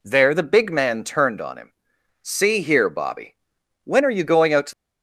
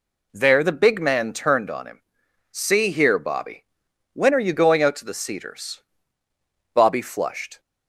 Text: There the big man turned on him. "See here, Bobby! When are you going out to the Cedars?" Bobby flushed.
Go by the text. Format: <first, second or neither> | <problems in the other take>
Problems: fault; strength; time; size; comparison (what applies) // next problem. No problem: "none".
second | stops before "the Cedars Bobby flushed"; at 4.7 s